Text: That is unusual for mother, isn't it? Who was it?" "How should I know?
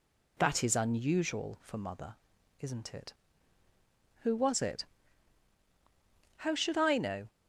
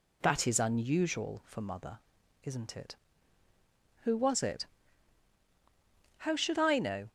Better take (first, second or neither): neither